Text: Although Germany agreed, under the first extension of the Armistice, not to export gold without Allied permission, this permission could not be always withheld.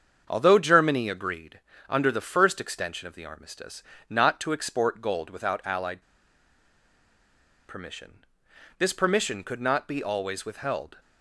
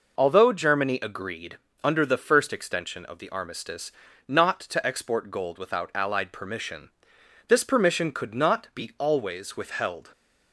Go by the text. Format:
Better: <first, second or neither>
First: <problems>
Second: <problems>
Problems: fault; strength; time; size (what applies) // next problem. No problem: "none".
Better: second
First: starts louder than the rest; strong; until 1.2 s; 7 dB // pauses between "Allied" and "permission"; strong; at 6.0 s; 1.6 s long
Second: none